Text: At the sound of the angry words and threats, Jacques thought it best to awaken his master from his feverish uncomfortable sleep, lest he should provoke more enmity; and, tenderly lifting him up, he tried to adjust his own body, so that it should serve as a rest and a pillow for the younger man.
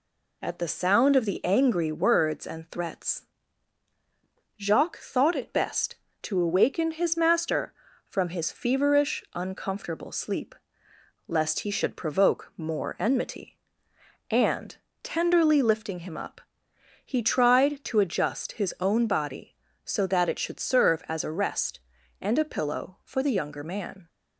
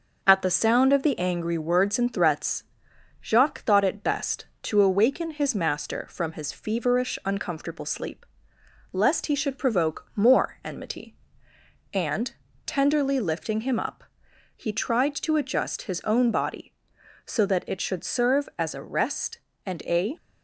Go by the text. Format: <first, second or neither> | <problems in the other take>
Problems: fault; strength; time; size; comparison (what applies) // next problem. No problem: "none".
first | stops before "pillow for the younger man"; at 20.1 s